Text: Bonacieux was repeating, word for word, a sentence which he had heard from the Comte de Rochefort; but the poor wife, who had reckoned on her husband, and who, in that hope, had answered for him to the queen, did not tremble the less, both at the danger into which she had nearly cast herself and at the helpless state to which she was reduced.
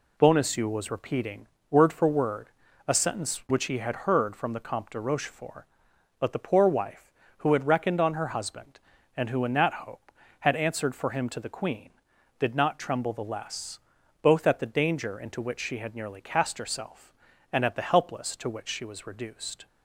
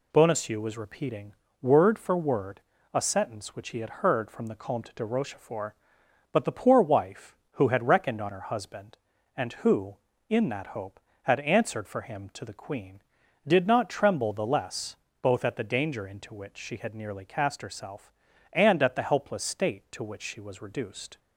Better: second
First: skips "state"; at 18.3 s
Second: none

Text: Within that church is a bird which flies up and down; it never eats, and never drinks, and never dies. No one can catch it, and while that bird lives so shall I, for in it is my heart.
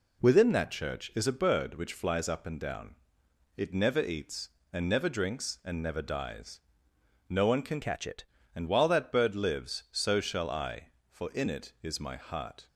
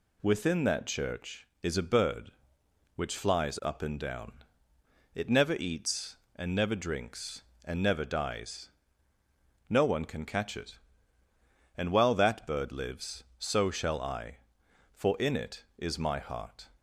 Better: second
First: changes voice from "catch" to "it"; from 7.8 to 8.2 s; 0.4 s long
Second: none

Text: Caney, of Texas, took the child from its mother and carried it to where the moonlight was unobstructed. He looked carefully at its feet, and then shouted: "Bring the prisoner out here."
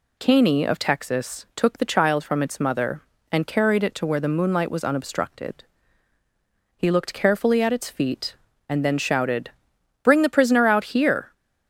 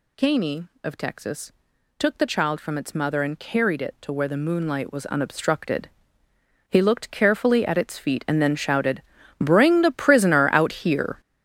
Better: first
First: none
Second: gets louder; strong; throughout; 10.5 dB

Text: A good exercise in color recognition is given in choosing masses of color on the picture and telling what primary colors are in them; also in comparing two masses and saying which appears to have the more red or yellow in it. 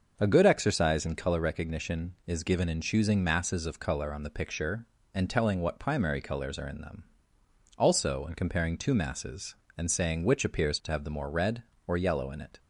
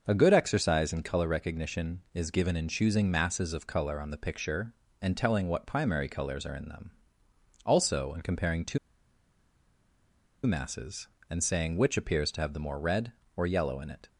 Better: first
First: starts louder than the rest; until 1.1 s; 6.5 dB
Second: starts louder than the rest; until 1.0 s; 6.5 dB // pauses between "two" and "masses"; strong; at 8.7 s; 1.6 s long

